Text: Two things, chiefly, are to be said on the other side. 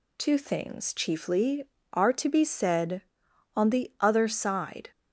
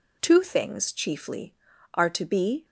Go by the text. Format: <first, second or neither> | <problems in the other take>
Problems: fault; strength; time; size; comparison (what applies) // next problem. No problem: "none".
first | stops before "said on the other side"; at 2.6 s